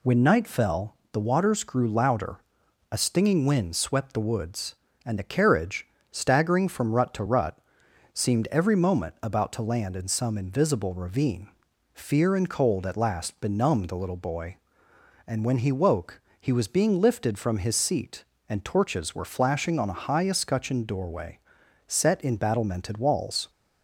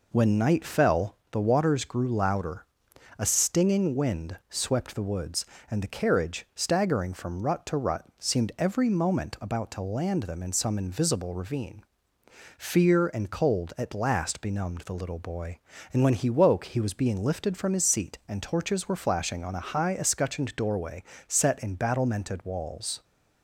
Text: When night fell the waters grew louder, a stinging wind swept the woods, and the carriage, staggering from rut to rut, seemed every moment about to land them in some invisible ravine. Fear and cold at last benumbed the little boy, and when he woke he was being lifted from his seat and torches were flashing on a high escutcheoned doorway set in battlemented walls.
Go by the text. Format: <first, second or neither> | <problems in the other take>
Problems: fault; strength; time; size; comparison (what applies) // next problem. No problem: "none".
second | pauses between "fell" and "the"; slight; at 0.9 s; 0.16 s long // skips "them"; at 9.9 s // pauses between "woke" and "he"; slight; at 16.2 s; 0.18 s long // pauses between "doorway" and "set"; noticeable; at 21.3 s; 0.48 s long; slight in the second